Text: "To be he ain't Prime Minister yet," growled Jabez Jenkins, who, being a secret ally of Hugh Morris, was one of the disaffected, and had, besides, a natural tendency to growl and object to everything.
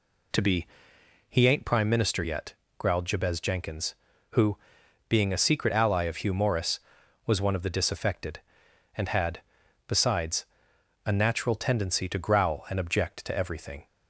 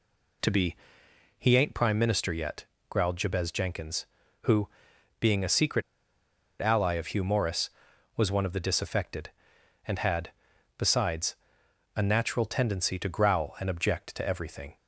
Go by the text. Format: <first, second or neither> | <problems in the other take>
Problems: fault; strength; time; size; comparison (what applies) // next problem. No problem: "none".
first | pauses between "be" and "he"; noticeable; at 0.7 s; 0.62 s long; noticeable in the first // pauses between "secret" and "ally"; noticeable; at 5.8 s; 0.79 s long